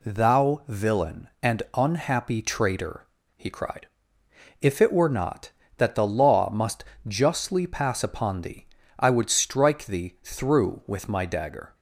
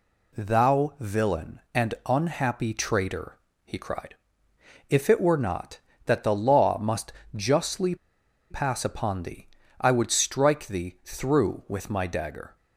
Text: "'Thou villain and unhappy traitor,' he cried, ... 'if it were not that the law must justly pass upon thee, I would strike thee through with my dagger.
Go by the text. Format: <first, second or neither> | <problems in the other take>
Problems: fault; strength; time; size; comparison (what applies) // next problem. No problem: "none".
first | pauses between "must" and "justly"; slight; at 7.1 s; 0.22 s long; slight in the first // pauses between "justly" and "pass"; noticeable; at 7.9 s; 0.55 s long